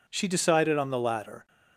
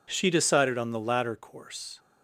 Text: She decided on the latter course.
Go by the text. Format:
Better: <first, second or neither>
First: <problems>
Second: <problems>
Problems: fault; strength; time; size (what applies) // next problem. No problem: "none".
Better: second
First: stops before "course"; at 1.4 s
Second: none